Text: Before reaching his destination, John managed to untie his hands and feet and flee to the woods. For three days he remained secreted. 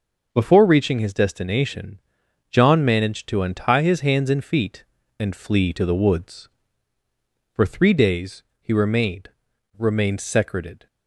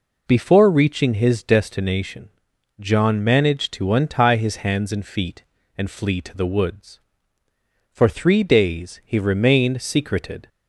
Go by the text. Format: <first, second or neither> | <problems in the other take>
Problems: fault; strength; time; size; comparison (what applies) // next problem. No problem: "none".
second | pauses between "days" and "he"; slight; at 8.4 s; 0.18 s long // says "remained" twice; at 9.7 s